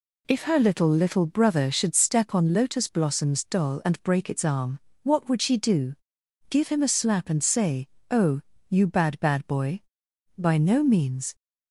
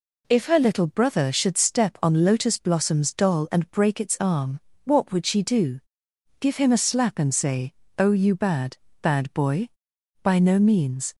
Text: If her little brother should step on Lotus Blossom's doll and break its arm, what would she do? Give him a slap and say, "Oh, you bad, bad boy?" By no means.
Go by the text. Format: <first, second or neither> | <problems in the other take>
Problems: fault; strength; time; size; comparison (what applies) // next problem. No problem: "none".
second | says "little" twice; at 0.8 s